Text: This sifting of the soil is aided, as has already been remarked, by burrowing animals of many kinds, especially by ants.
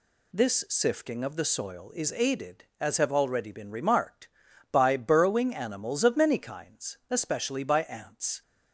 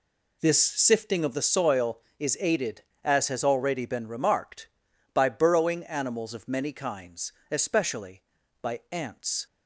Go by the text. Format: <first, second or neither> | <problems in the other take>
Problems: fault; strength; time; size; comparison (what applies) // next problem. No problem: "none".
second | says "have" for "has"; at 2.9 s